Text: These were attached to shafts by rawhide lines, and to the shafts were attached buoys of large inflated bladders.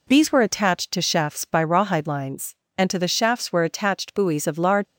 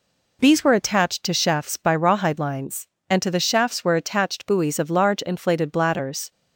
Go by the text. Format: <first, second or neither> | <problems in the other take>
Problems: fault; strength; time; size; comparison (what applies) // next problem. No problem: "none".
second | stops before "inflated bladders"; at 4.8 s